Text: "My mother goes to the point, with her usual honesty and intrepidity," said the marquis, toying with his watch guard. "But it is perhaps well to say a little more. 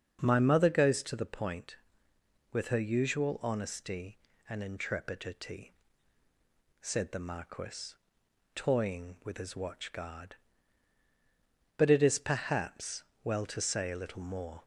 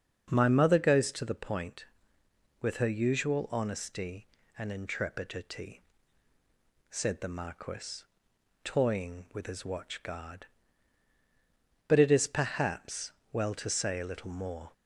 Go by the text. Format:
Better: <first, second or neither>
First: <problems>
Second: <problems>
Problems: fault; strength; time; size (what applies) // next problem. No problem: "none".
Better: neither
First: starts louder than the rest; until 1.2 s; 6.5 dB // pauses between "perhaps" and "well"; slight; at 13.0 s; 0.18 s long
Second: starts louder than the rest; until 1.3 s; 6.5 dB // pauses between "perhaps" and "well"; slight; at 13.1 s; 0.18 s long